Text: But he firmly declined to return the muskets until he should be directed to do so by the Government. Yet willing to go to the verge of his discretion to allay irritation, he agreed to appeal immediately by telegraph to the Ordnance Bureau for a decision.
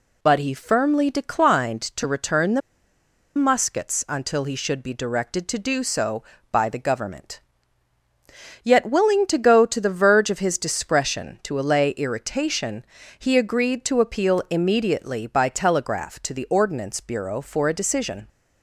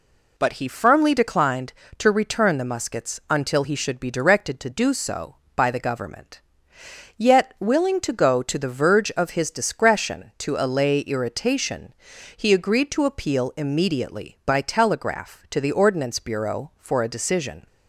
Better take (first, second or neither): second